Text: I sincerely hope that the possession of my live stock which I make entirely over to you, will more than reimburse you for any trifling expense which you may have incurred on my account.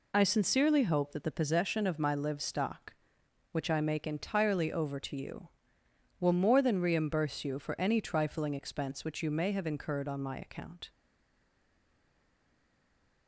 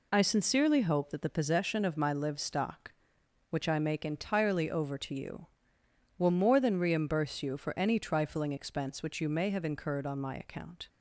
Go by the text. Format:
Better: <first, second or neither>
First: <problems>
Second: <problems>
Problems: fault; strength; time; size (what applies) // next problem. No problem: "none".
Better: second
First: stays silent after the last word; from 10.8 s on; 2.4 s long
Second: none